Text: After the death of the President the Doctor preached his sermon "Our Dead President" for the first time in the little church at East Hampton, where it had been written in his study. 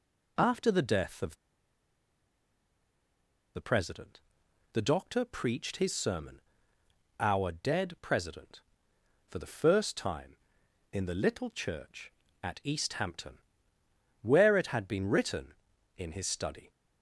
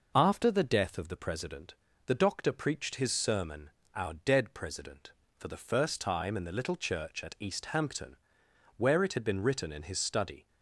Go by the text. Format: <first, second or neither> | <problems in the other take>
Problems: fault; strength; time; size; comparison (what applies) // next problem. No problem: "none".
second | pauses between "of" and "the"; strong; at 1.3 s; 2.2 s long // pauses between "President" and "the"; noticeable; at 4.1 s; 0.54 s long; slight in the second // pauses between "sermon" and "Our"; noticeable; at 6.3 s; 0.78 s long; slight in the second